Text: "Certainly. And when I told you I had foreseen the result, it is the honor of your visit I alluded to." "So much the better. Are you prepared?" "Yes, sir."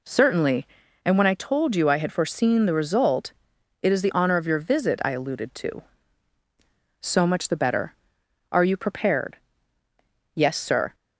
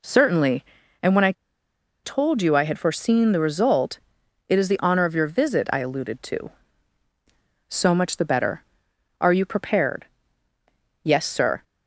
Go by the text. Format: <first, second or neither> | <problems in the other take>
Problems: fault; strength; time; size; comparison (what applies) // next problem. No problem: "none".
first | pauses between "I" and "told"; noticeable; at 1.3 s; 0.71 s long